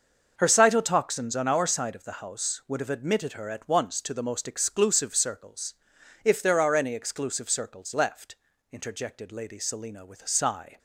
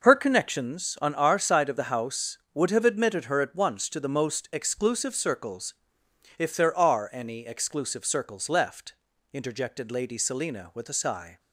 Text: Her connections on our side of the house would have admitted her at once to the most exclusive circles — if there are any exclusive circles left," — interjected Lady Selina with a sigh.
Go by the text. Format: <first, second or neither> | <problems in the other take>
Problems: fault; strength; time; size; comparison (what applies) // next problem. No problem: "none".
second | starts louder than the rest; until 1.3 s; 6 dB // says "cytotoxins" for "connections"; at 0.4 s